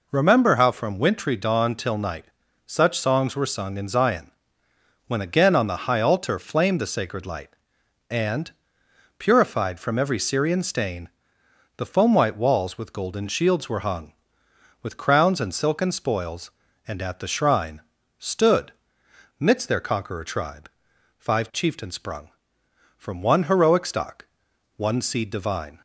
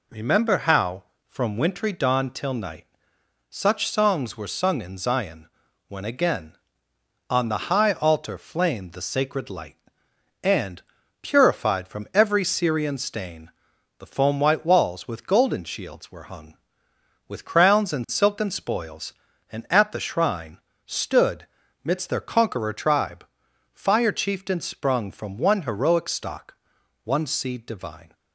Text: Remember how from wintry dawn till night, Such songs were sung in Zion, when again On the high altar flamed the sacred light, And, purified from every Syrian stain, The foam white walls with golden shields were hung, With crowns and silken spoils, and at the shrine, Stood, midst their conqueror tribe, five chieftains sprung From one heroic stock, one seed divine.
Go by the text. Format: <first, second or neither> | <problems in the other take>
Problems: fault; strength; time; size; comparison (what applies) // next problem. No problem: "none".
first | says "fire" for "five"; at 23.7 s